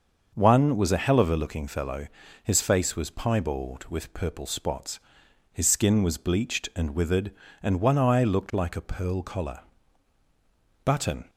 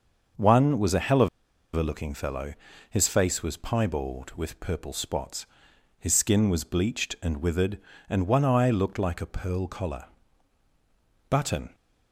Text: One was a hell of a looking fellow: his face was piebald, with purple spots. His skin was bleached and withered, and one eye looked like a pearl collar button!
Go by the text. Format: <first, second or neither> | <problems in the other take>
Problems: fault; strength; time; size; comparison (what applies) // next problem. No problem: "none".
first | starts louder than the rest; until 1.8 s; 6.5 dB; also in the first // pauses between "of" and "a"; noticeable; at 1.2 s; 0.47 s long // pauses between "collar" and "button"; at 10.0 s; 1.2 s long; also in the first